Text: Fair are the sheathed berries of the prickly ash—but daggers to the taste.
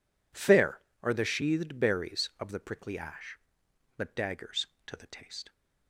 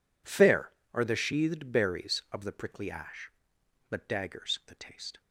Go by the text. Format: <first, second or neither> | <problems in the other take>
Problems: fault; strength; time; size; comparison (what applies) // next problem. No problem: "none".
first | skips "to"; at 4.6 s